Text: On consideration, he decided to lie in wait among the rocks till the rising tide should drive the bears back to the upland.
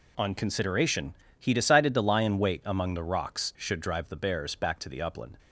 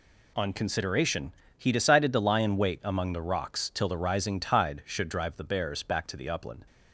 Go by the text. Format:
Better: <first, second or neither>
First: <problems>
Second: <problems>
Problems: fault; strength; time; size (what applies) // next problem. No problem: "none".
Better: second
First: skips "till the rising tide"; at 3.5 s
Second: none